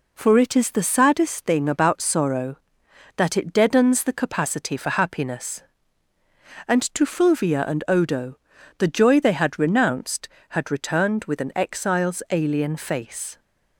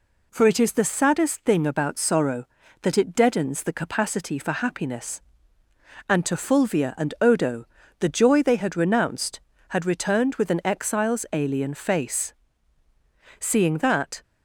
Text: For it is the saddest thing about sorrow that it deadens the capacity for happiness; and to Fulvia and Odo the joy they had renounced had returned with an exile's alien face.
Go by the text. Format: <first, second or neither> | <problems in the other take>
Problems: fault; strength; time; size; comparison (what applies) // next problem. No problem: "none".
first | pauses between "Odo" and "the"; slight; at 7.6 s; 0.32 s long; also in the first // goes on to say "Seeing that"; noticeable; from 13.4 s on; 0.82 s long